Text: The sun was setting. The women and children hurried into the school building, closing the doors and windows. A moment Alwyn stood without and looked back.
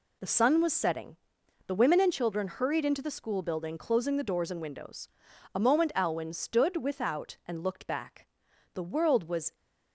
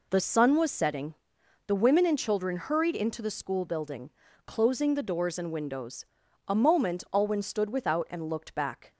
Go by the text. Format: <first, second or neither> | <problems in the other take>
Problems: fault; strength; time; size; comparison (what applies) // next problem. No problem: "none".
second | goes on to say "The world was"; noticeable; from 8.7 s on; 0.80 s long